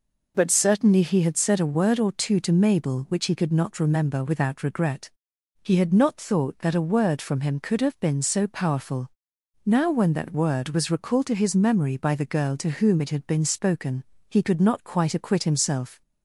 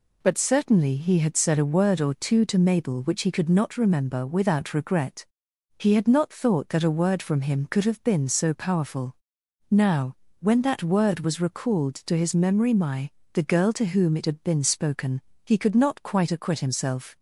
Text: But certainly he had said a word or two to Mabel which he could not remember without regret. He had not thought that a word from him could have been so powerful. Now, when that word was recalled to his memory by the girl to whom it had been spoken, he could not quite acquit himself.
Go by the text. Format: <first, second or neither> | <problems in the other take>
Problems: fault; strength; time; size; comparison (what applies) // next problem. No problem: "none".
first | says "my" for "by"; at 12.7 s